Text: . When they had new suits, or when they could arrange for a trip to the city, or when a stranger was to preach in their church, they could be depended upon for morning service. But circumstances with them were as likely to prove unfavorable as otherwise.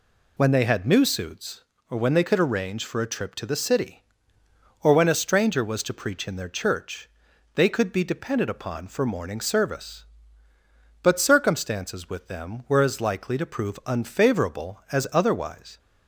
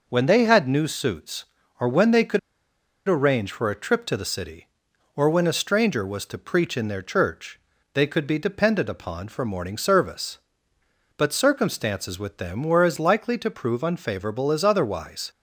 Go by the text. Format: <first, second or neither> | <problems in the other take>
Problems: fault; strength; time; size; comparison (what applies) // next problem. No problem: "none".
first | pauses between "could" and "arrange"; noticeable; at 2.3 s; 0.68 s long